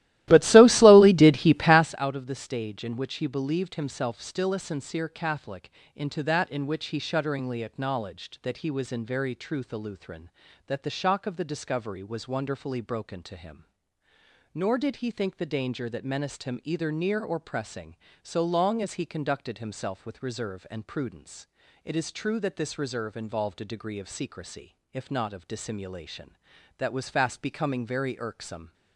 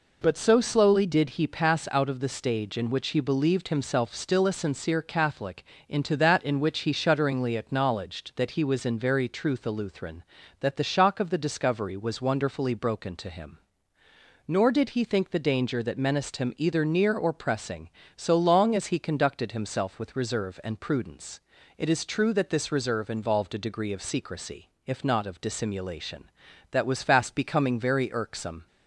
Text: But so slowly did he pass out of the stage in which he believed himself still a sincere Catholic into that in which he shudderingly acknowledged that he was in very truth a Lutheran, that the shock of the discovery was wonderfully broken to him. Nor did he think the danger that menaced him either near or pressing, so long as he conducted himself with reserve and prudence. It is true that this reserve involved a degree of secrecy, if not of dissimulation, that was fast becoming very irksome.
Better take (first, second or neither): second